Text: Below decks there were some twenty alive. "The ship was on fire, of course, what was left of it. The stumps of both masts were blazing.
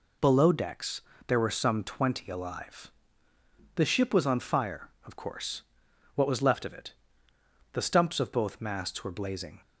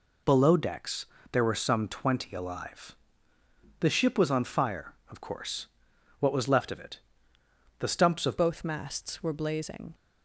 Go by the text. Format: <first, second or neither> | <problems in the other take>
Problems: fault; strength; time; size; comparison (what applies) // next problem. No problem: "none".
first | pauses between "decks" and "there"; slight; at 1.0 s; 0.28 s long; slight in the first // changes voice at "both"; from 8.3 s on; 1.6 s long